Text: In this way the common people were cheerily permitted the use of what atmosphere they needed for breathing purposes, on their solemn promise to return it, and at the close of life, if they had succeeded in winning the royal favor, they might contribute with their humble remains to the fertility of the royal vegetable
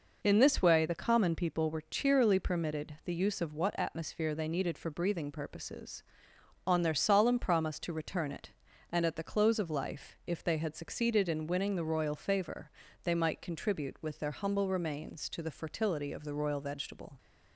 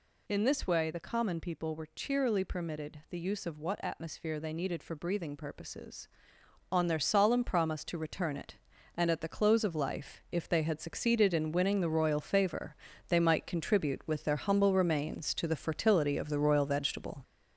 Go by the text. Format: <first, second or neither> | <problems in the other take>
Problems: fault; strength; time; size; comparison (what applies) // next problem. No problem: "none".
first | gets louder; noticeable; throughout; 5 dB